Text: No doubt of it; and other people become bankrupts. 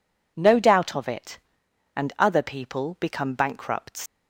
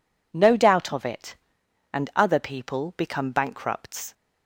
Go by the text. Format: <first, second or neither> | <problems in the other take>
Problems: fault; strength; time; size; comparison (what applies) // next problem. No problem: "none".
second | leaves "bankrupts" unfinished; at 4.0 s; 100 ms